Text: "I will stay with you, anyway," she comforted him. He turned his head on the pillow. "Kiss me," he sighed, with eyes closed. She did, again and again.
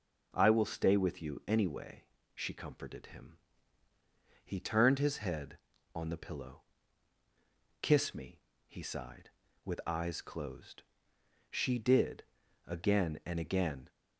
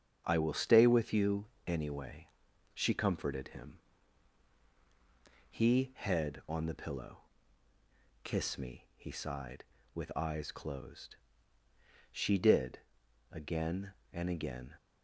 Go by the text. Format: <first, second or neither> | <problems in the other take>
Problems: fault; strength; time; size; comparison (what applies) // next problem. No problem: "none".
first | starts louder than the rest; strong; until 1.2 s; 7.5 dB // skips "turned his"; at 5.9 s